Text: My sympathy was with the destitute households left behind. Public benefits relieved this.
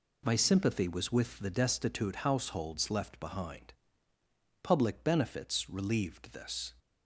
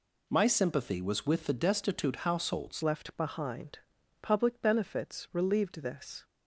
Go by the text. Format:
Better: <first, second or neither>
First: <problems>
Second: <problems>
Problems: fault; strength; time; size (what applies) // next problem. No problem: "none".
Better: first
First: none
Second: changes voice at "left"; from 2.8 s on; 3.4 s long